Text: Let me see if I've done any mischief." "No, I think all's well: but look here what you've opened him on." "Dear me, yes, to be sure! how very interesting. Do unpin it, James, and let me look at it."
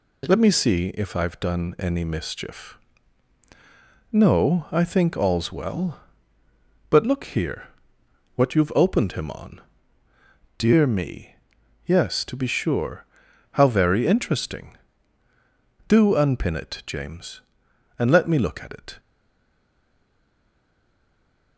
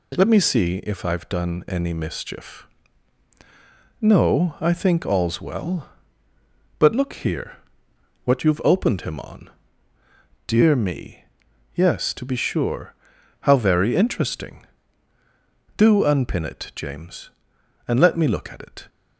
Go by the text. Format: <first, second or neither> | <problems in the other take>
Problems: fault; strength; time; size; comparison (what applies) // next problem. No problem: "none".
second | pauses between "here" and "what"; noticeable; at 7.6 s; 0.68 s long; noticeable in the second // stays silent after the last word; strong; from 18.9 s on; 2.6 s long